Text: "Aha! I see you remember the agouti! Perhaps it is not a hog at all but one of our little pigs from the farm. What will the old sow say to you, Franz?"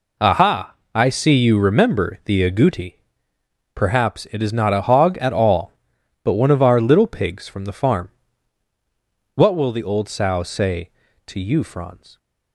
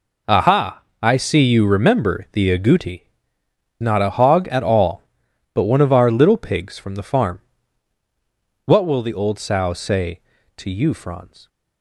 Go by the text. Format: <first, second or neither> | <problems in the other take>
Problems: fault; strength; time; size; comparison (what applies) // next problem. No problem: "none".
first | skips "Perhaps it is"; at 3.4 s